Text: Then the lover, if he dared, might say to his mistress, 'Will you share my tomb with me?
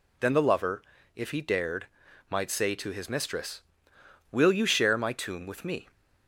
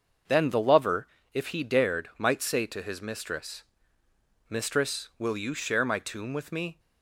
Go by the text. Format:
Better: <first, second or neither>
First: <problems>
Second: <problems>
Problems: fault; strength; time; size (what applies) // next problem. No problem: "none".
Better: first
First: none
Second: starts louder than the rest; until 1.5 s; 6 dB // says "mistress" twice; at 4.4 s